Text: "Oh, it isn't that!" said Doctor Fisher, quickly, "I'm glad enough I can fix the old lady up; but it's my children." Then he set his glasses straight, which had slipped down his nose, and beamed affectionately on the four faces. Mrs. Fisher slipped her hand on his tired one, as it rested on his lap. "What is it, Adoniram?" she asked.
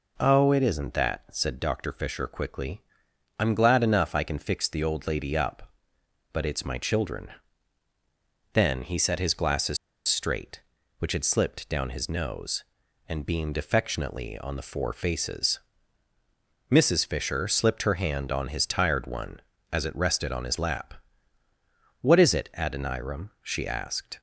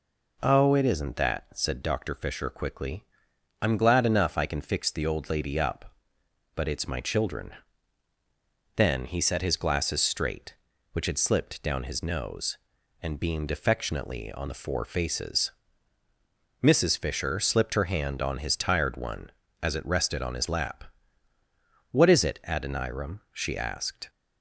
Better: second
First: pauses between "glasses" and "straight"; slight; at 9.7 s; 0.30 s long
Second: none

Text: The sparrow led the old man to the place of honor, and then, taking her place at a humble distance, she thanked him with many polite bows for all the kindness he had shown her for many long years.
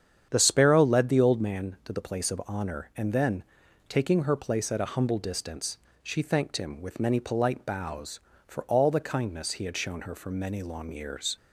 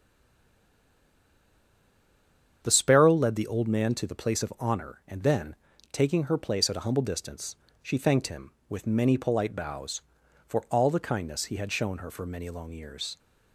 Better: first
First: starts louder than the rest; strong; until 1.3 s; 8.5 dB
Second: stays silent before the first word; strong; until 2.6 s; 2.6 s long // starts louder than the rest; strong; until 3.6 s; 8 dB

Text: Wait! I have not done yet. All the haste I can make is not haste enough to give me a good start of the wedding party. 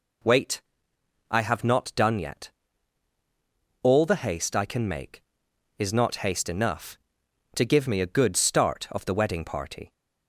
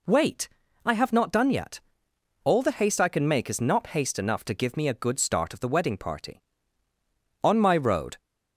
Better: first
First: none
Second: goes on to say "On my road"; noticeable; from 7.4 s on; 0.74 s long

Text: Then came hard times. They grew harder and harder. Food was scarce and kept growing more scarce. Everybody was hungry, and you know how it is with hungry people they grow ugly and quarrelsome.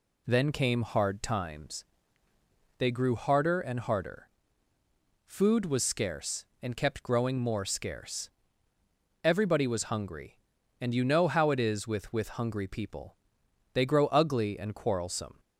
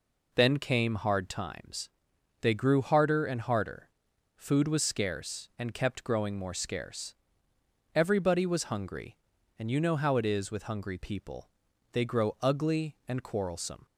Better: second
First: says "with" twice; at 12.1 s // pauses between "people" and "they"; noticeable; at 13.1 s; 0.56 s long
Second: pauses between "people" and "they"; at 11.4 s; 0.44 s long

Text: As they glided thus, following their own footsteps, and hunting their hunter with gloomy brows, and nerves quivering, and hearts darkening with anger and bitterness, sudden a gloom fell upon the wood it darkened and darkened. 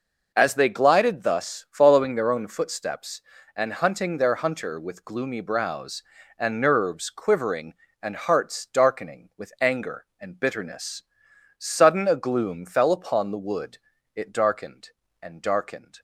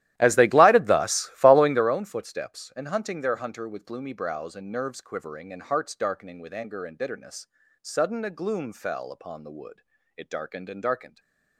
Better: first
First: pauses between "wood" and "it"; at 13.7 s; 0.38 s long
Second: starts louder than the rest; strong; until 2.0 s; 14 dB // pauses between "wood" and "it"; slight; at 9.8 s; 0.34 s long // stays silent after the last word; slight; from 11.0 s on; 0.5 s long

